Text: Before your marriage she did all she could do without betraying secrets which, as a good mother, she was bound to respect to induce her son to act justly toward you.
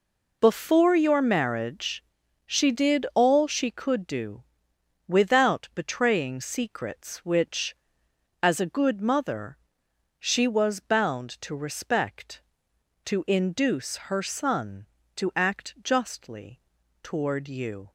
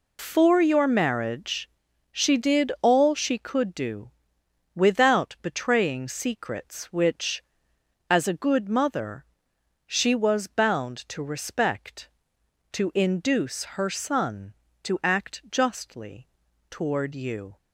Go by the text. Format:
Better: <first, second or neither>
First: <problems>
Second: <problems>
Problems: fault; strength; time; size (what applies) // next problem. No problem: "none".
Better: first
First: pauses between "marriage" and "she"; at 2.0 s; 0.42 s long // pauses between "do" and "without"; noticeable; at 4.4 s; 0.64 s long // pauses between "justly" and "toward"; at 16.5 s; 0.44 s long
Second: loses the start of "Before"; at 0.1 s; 125 ms // pauses between "marriage" and "she"; at 1.6 s; 0.42 s long // pauses between "do" and "without"; noticeable; at 4.1 s; 0.64 s long // pauses between "justly" and "toward"; at 16.2 s; 0.44 s long